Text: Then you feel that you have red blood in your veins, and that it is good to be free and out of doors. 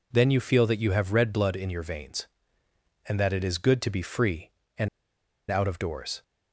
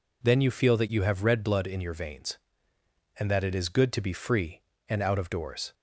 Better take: second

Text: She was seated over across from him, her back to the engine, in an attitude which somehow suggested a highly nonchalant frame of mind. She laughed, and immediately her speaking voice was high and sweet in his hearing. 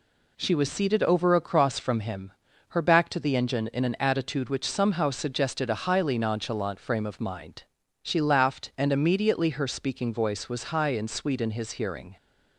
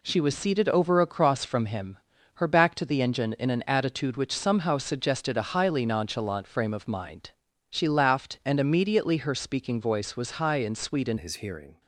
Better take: first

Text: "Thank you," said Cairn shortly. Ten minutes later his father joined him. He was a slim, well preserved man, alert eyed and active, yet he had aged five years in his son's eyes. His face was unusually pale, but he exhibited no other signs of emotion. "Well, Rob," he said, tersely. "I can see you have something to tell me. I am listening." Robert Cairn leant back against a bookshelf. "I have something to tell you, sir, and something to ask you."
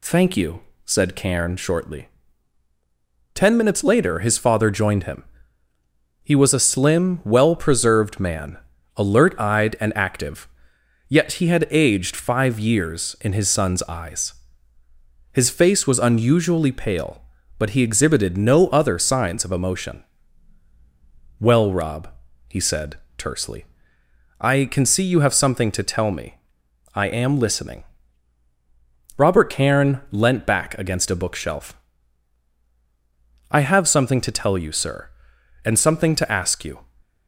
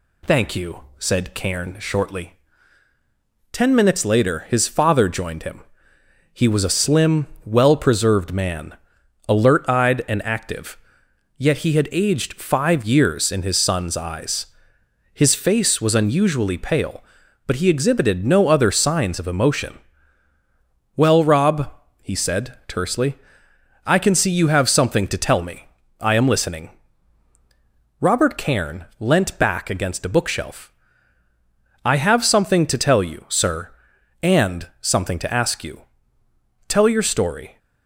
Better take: first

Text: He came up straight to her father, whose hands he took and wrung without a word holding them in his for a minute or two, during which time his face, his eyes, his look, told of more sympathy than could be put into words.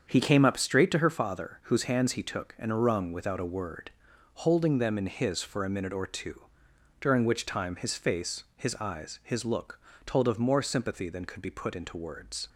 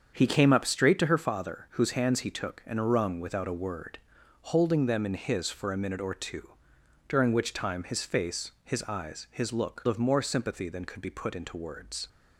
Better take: first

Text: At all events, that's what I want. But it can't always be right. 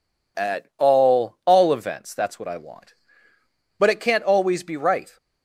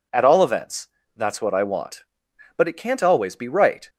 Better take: second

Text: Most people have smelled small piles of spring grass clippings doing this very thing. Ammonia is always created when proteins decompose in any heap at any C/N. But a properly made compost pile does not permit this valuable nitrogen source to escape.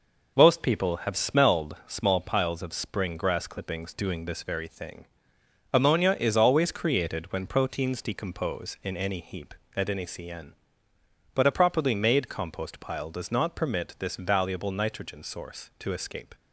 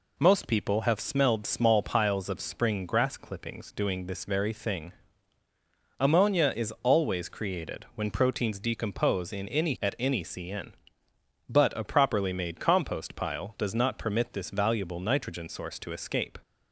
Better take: first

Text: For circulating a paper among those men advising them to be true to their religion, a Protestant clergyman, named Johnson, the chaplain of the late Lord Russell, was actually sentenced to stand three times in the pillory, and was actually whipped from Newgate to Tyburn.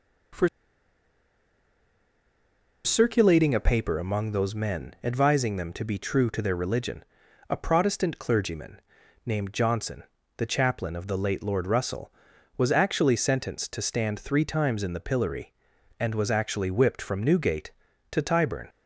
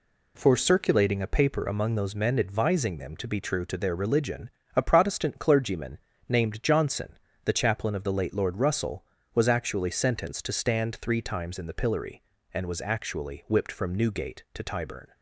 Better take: second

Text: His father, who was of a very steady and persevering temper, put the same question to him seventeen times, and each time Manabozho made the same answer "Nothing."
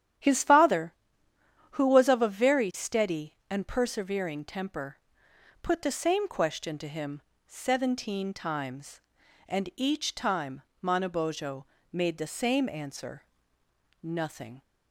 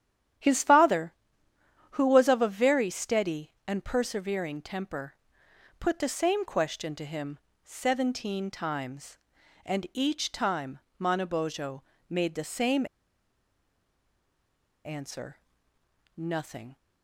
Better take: first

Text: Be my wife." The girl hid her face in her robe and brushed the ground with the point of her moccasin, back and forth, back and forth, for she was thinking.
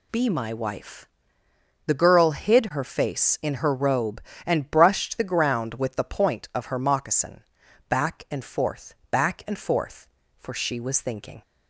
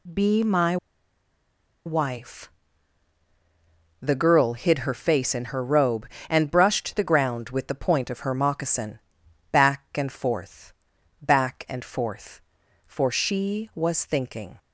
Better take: first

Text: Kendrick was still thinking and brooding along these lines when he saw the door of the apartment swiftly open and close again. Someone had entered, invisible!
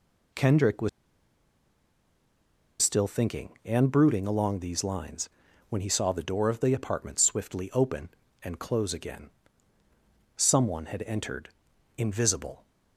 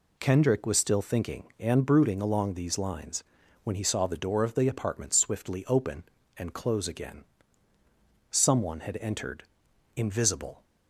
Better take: second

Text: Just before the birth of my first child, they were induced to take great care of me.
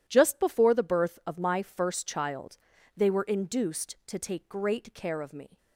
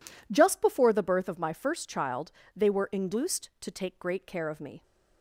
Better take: neither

